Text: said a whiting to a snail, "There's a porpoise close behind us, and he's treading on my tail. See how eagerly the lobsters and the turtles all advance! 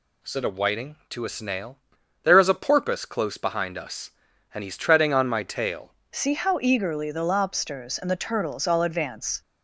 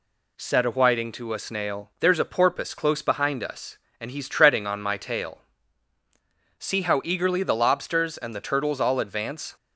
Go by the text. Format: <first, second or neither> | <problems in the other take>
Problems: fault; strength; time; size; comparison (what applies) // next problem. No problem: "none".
second | changes voice at "See"; from 6.1 s on; 3.3 s long